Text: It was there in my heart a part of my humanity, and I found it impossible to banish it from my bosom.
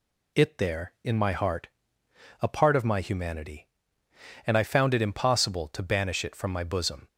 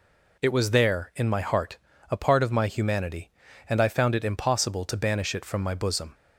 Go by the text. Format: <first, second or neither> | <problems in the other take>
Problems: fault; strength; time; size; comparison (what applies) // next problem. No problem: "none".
second | skips "was"; at 0.5 s // pauses between "heart" and "a"; noticeable; at 1.6 s; 0.74 s long; slight in the second